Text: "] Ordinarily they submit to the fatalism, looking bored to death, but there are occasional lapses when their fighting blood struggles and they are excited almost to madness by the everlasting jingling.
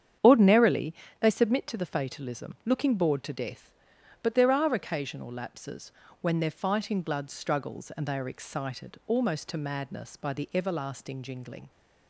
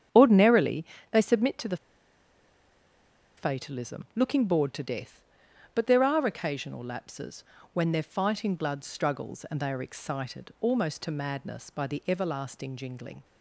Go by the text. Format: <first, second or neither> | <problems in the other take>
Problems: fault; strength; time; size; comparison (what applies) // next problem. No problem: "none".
first | starts louder than the rest; strong; until 1.3 s; 8.5 dB; strong in the first // pauses between "Ordinarily" and "they"; slight; at 0.8 s; 0.26 s long; slight in the first // pauses between "the" and "fatalism"; strong; at 1.7 s; 1.6 s long // pauses between "lapses" and "when"; slight; at 7.4 s; 0.30 s long; slight in the first